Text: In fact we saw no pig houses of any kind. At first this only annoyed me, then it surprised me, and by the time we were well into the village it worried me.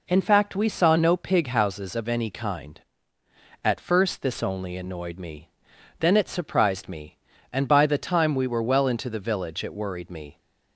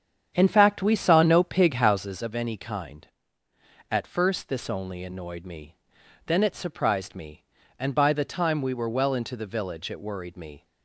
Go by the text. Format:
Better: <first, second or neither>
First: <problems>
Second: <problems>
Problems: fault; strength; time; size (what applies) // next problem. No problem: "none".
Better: first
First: none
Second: starts louder than the rest; strong; until 2.3 s; 8 dB